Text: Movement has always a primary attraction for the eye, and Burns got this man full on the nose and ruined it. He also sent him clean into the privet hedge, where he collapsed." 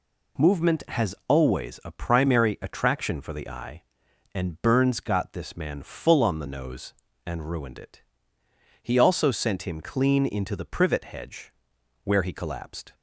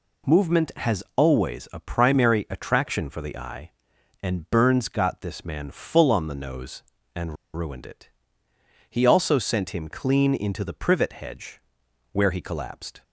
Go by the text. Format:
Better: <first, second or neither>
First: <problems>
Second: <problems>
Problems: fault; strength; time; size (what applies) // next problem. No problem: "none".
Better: first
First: none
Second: pauses between "and" and "ruined"; slight; at 7.3 s; 0.21 s long